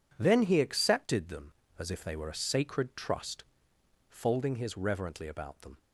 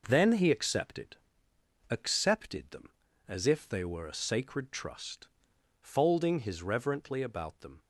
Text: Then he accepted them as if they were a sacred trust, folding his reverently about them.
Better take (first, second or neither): first